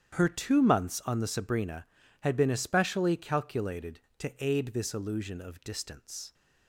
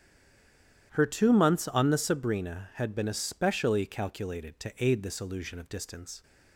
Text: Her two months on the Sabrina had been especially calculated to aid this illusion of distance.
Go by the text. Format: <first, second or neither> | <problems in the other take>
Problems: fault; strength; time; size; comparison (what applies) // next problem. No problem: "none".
first | stays silent before the first word; slight; until 0.9 s; 0.9 s long // starts louder than the rest; strong; until 1.9 s; 10 dB; strong in the first